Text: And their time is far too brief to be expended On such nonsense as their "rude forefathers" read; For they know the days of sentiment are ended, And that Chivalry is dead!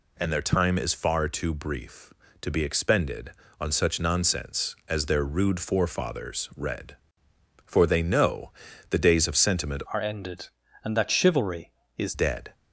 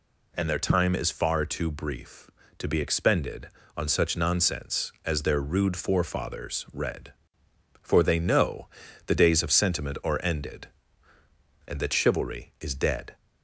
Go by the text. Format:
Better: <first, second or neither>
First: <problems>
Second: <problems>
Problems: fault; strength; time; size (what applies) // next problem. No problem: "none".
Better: second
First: pauses between "know" and "the"; at 8.5 s; 0.40 s long // changes voice from "are" to "is"; from 9.9 to 12.1 s; 2.2 s long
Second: pauses between "know" and "the"; at 8.6 s; 0.40 s long